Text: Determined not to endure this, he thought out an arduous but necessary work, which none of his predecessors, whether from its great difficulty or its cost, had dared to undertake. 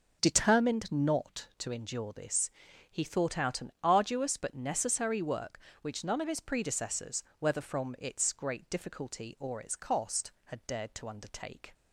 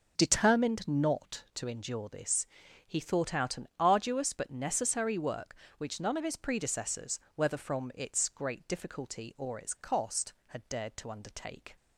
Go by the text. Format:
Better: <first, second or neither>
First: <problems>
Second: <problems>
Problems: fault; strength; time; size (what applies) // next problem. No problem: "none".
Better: neither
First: none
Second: none